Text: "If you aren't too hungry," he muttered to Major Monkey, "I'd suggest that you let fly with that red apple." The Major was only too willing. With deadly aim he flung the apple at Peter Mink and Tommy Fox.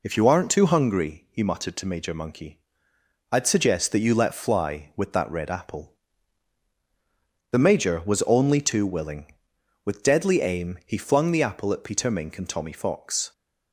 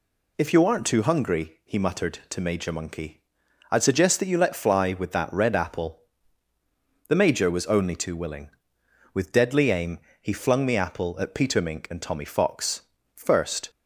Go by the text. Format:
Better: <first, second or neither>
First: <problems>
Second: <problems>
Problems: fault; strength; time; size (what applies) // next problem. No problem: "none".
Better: first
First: none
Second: pauses between "aim" and "he"; slight; at 9.9 s; 0.20 s long // goes on to say "First"; from 13.1 s on; 0.56 s long